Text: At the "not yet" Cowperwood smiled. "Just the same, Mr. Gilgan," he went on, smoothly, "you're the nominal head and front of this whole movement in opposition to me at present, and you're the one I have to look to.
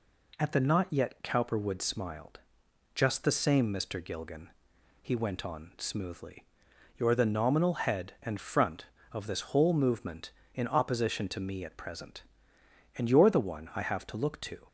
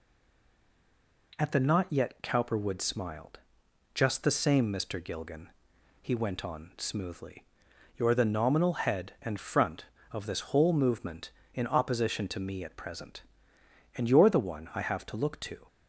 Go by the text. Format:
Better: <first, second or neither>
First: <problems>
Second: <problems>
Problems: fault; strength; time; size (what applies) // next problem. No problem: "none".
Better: first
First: none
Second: stays silent before the first word; noticeable; until 1.3 s; 1.3 s long